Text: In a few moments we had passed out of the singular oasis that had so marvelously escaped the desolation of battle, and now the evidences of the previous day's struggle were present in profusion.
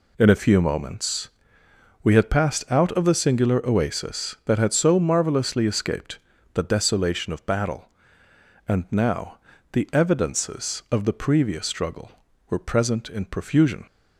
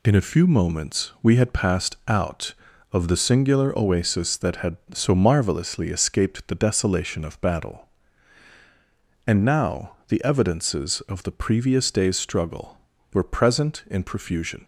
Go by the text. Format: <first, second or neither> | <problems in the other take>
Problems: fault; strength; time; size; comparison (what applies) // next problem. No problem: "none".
second | pauses between "moments" and "we"; noticeable; at 1.2 s; 0.76 s long // pauses between "escaped" and "the"; slight; at 6.1 s; 0.34 s long // pauses between "now" and "the"; slight; at 9.3 s; 0.34 s long // skips "day's"; at 11.6 s